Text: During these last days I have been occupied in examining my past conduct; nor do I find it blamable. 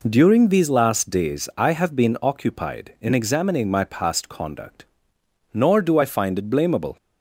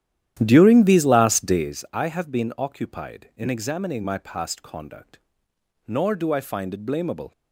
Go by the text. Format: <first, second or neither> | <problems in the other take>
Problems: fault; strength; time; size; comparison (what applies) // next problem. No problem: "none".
first | starts louder than the rest; strong; until 1.8 s; 11.5 dB